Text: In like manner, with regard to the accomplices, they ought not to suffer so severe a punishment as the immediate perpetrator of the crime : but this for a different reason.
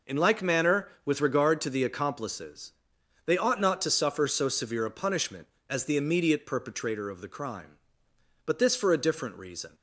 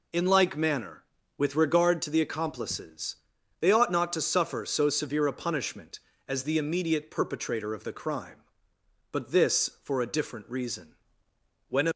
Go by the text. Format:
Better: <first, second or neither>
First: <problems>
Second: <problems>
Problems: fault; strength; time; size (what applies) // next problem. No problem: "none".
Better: first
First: none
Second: goes on to say "When a"; slight; from 11.6 s on; 0.22 s long